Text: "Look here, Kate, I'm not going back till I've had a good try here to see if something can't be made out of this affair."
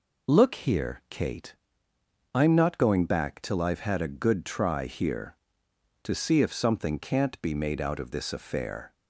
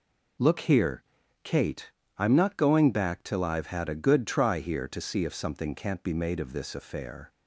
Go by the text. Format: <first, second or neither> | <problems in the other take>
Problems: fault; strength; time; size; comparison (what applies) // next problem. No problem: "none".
first | skips "out"; at 6.3 s